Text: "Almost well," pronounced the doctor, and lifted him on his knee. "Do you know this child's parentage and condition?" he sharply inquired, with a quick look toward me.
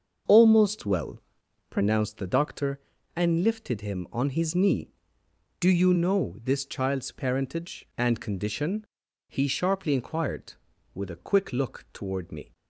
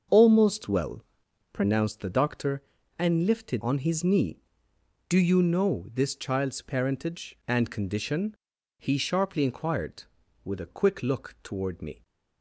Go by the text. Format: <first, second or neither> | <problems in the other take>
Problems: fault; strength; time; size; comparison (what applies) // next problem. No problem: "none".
first | starts louder than the rest; until 1.6 s; 6.5 dB; also in the first // skips "him"; at 3.6 s